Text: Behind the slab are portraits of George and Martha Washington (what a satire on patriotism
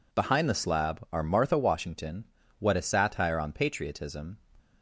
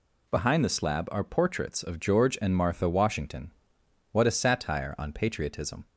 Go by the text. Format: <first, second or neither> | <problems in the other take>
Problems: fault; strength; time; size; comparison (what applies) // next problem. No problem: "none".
second | skips "portraits of George and"; at 1.2 s